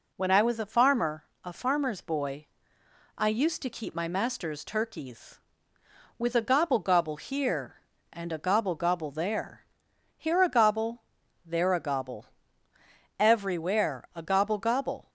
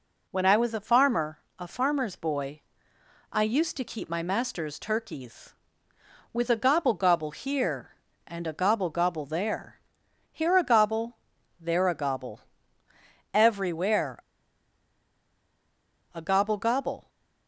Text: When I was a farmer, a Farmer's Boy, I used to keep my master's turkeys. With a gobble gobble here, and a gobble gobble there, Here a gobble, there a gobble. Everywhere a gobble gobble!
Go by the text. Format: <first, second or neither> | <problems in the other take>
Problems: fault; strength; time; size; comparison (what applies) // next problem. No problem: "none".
first | pauses between "Everywhere" and "a"; strong; at 14.1 s; 1.9 s long